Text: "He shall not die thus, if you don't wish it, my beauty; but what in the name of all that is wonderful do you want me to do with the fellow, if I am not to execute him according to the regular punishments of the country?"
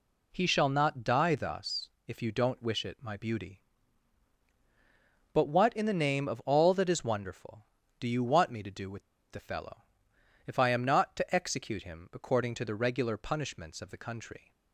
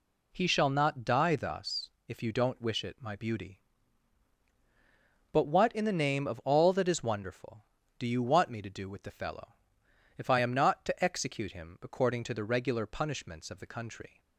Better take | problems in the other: second | pauses between "with" and "the"; slight; at 9.0 s; 0.29 s long

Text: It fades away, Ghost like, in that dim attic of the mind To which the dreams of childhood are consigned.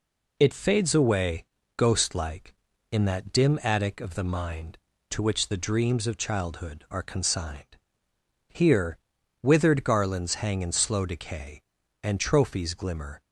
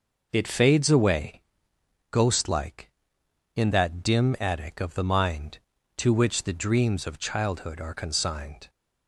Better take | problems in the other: second | goes on to say "Here withered garlands hang in slow decay And trophies glimmer"; strong; from 8.4 s on; 4.7 s long

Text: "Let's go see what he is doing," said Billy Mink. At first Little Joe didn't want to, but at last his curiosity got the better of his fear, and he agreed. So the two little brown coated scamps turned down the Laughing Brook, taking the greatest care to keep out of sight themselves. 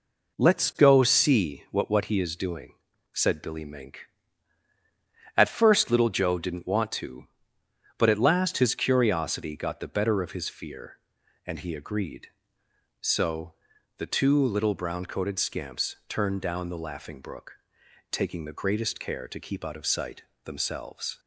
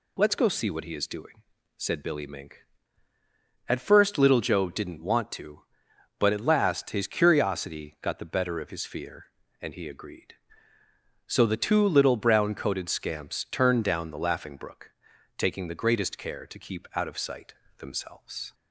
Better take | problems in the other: second | says "what" twice; at 1.8 s // pauses between "So" and "the"; at 13.5 s; 0.42 s long // pauses between "sight" and "themselves"; slight; at 20.2 s; 0.20 s long; slight in the second

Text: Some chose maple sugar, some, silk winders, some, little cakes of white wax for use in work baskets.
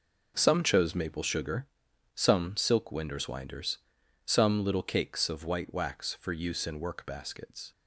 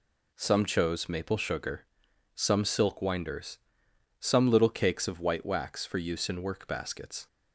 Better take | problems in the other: second | says "winders" twice; at 3.2 s

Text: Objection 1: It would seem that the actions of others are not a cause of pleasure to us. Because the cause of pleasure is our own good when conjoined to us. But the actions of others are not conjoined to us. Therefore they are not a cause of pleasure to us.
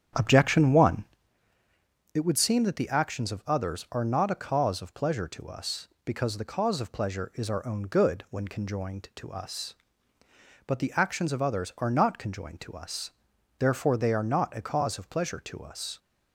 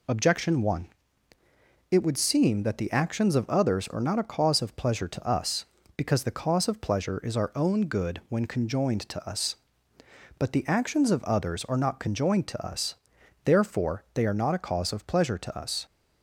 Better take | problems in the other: second | starts louder than the rest; strong; until 1.3 s; 9 dB

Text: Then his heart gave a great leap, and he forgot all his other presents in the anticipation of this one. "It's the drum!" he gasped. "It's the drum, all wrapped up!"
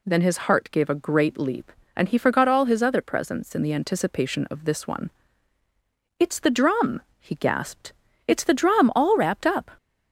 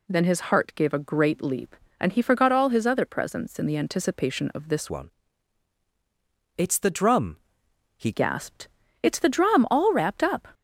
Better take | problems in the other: first | changes voice from "one" to "he"; from 4.8 to 8.1 s; 3.3 s long

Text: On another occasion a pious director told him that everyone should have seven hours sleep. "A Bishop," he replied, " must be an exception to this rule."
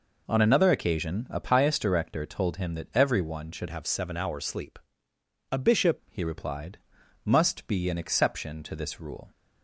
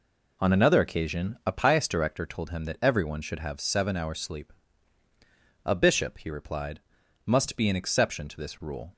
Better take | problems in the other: second | changes voice from "have" to "Bishop"; from 3.6 to 5.9 s; 2.3 s long

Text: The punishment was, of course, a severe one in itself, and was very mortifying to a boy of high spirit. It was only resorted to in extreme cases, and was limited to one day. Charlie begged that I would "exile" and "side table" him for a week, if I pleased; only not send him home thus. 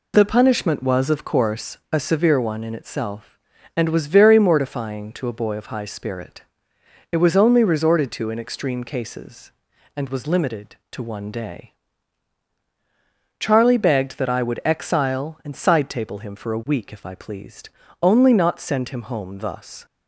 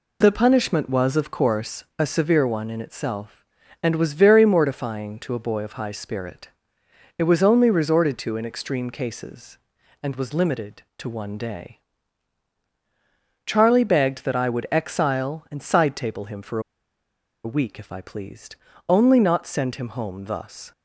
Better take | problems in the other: first | pauses between "for" and "a"; noticeable; at 16.5 s; 0.84 s long

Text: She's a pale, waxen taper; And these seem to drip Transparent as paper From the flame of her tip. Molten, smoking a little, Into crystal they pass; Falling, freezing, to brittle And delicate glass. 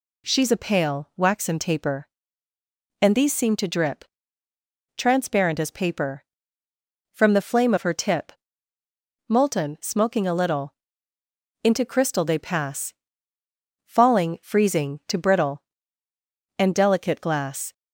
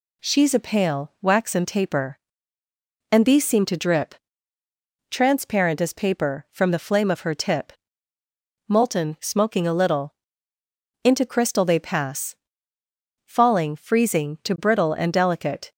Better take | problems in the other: first | pauses between "drip" and "Transparent"; noticeable; at 4.1 s; 0.94 s long; noticeable in the first // stops before "glass"; at 15.7 s

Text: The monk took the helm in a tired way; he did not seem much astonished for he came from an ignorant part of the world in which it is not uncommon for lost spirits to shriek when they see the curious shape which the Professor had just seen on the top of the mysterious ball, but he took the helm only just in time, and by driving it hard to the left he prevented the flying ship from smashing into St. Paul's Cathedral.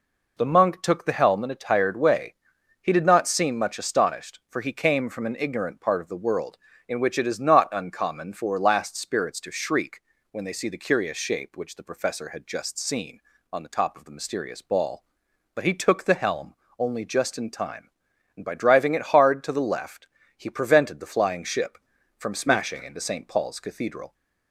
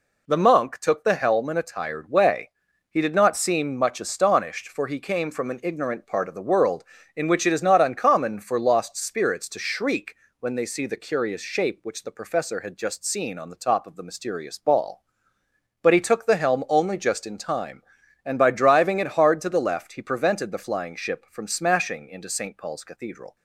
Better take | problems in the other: second | says "last" for "lost"; at 8.5 s // pauses between "shriek" and "when"; slight; at 9.9 s; 0.30 s long; slight in the second // pauses between "helm" and "only"; slight; at 16.5 s; 0.24 s long // pauses between "left" and "he"; slight; at 20.0 s; 0.32 s long

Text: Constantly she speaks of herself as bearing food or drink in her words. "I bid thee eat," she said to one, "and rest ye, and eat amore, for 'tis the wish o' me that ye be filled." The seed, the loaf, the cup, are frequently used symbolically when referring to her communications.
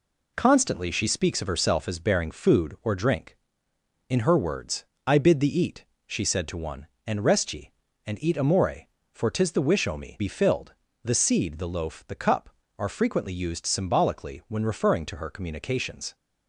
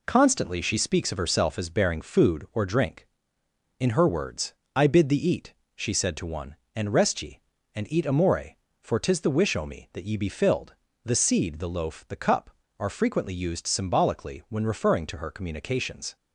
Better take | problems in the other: second | skips "that ye"; at 10.1 s

